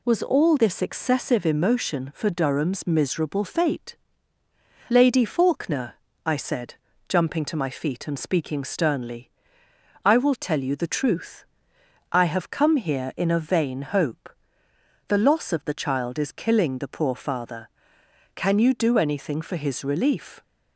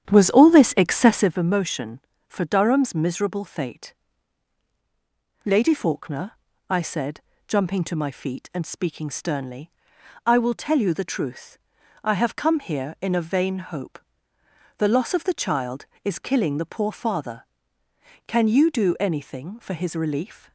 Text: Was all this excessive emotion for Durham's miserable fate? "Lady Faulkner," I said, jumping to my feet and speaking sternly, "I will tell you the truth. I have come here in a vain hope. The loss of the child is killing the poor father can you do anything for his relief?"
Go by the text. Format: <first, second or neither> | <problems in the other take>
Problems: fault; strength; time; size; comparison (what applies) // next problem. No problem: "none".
first | starts louder than the rest; strong; until 1.3 s; 9.5 dB